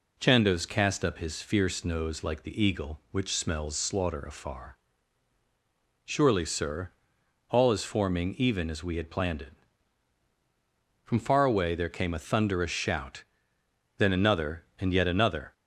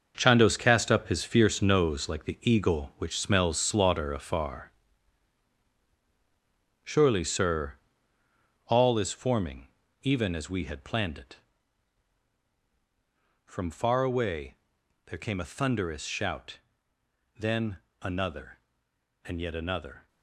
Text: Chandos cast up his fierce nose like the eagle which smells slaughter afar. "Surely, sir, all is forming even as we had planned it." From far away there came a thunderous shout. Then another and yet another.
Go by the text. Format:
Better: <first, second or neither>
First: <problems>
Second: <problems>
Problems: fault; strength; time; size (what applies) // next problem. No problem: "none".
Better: first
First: none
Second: gets quieter; strong; throughout; 11 dB // pauses between "forming" and "even"; slight; at 9.6 s; 0.34 s long // pauses between "away" and "there"; noticeable; at 14.5 s; 0.50 s long // pauses between "Then" and "another"; slight; at 17.7 s; 0.22 s long